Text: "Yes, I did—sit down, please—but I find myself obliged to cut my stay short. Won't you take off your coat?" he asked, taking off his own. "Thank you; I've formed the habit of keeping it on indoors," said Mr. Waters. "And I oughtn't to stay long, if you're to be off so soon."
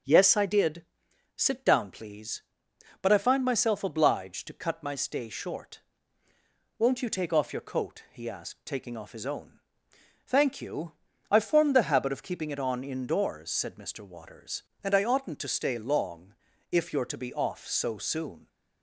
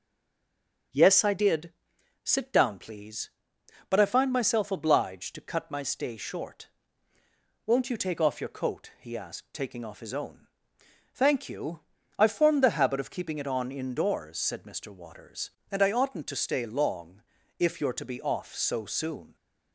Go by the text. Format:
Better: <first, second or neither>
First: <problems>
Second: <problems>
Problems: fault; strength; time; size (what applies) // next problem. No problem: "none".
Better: first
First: starts louder than the rest; until 1.5 s; 7 dB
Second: stays silent before the first word; slight; until 0.9 s; 0.9 s long // starts louder than the rest; until 2.4 s; 7 dB